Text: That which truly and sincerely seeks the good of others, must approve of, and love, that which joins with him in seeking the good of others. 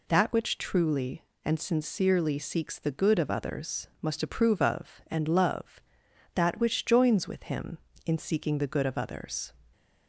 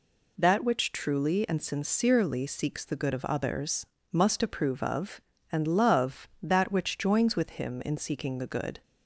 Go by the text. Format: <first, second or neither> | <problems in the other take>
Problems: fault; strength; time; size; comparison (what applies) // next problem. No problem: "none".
first | stops before "of others"; at 8.8 s